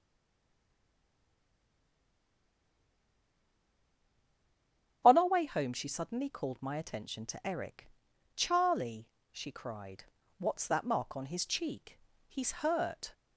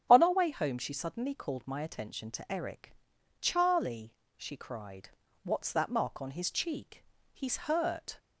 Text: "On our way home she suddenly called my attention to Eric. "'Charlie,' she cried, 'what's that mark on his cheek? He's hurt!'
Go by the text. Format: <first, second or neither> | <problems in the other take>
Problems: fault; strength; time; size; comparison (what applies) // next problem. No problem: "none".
second | stays silent before the first word; strong; until 5.0 s; 5.0 s long // starts louder than the rest; strong; until 6.0 s; 7.5 dB; strong in the second